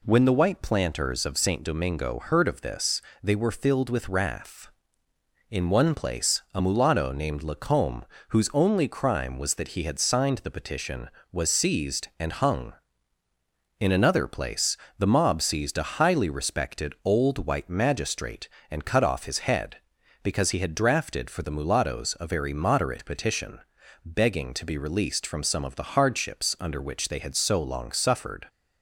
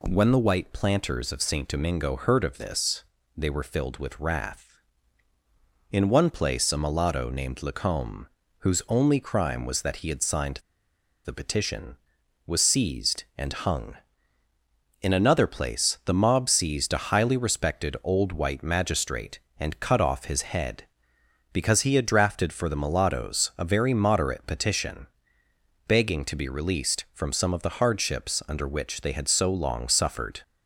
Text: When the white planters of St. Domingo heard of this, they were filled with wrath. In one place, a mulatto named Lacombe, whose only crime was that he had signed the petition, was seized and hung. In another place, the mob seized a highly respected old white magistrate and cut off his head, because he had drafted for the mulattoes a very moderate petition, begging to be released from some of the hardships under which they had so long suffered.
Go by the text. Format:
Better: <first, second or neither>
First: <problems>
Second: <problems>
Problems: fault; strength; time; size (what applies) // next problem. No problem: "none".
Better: first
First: none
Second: pauses between "signed" and "the"; noticeable; at 10.5 s; 0.66 s long